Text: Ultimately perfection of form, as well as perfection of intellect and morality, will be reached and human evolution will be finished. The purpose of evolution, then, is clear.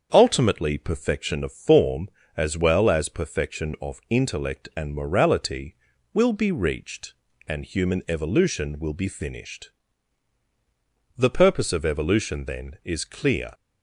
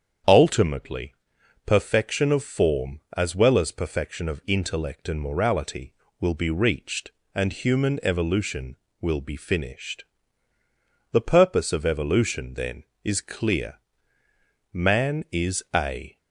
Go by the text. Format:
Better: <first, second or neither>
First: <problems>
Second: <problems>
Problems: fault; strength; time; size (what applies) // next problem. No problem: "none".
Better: first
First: starts louder than the rest; until 1.1 s; 7 dB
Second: starts louder than the rest; strong; until 1.7 s; 8 dB // pauses between "Ultimately" and "perfection"; noticeable; at 1.1 s; 0.50 s long // goes on to say "Man is a"; from 14.7 s on; 1.4 s long